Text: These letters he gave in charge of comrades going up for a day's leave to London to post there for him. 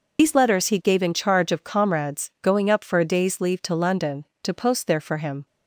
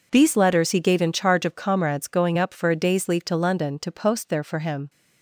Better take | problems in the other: second | loses the start of "These"; at 0.1 s; 85 ms

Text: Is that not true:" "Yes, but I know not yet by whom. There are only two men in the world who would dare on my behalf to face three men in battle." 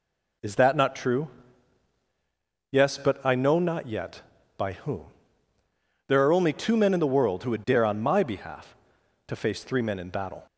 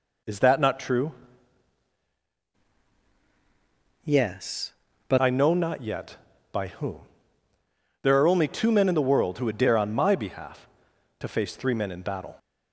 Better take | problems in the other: first | changes voice from "Yes" to "but"; from 4.0 to 5.1 s; 1.1 s long

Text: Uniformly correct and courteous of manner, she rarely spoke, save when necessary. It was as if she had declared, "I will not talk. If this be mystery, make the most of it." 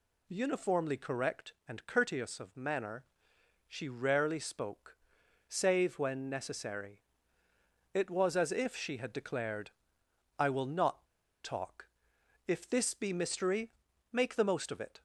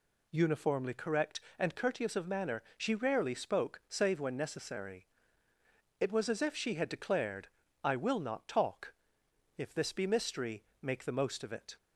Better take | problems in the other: second | pauses between "not" and "talk"; at 11.0 s; 0.37 s long

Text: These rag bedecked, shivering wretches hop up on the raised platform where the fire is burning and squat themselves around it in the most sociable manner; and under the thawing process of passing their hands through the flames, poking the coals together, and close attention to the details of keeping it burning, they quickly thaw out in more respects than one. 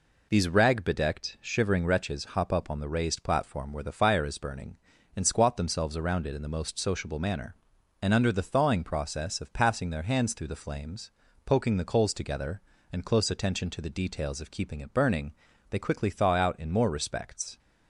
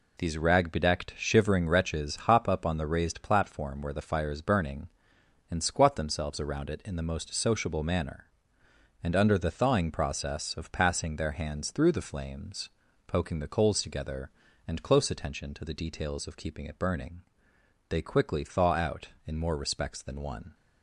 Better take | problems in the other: second | stops before "than one"; at 17.5 s

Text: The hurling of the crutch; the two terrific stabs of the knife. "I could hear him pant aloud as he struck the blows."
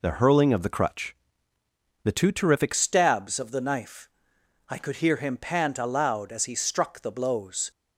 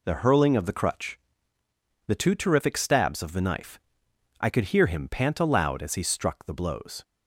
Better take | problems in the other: second | changes voice at "stabs"; from 2.7 s on; 5.0 s long

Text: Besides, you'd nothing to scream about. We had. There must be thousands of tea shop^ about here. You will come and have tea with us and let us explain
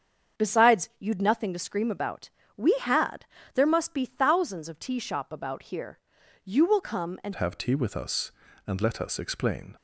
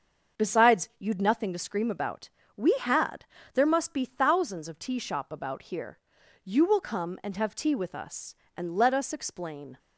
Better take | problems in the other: second | starts louder than the rest; strong; until 1.4 s; 7.5 dB; also in the second // changes voice at "have"; from 7.3 s on; 2.4 s long

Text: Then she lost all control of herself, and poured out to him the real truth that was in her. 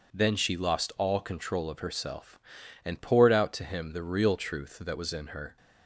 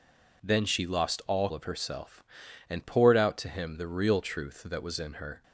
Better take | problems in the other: first | skips "control"; at 1.5 s

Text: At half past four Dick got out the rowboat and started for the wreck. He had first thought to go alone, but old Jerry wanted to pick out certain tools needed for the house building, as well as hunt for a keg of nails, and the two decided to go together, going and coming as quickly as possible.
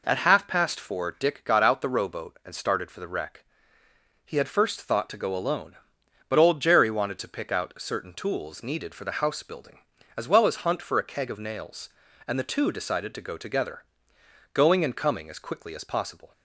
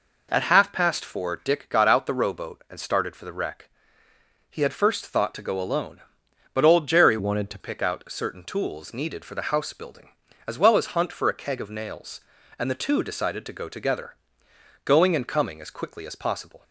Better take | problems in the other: first | changes voice from "wanted" to "to"; from 7.1 to 7.5 s; 0.4 s long

